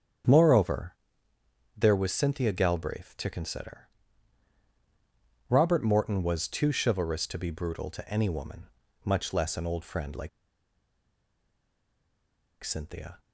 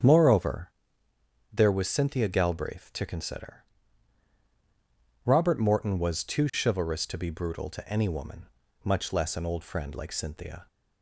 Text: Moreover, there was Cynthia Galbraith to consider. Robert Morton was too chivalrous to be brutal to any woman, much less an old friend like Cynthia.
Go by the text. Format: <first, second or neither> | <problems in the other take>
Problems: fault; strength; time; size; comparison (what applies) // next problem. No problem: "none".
second | starts louder than the rest; strong; until 2.1 s; 8.5 dB; strong in the second // pauses between "like" and "Cynthia"; strong; at 10.2 s; 2.3 s long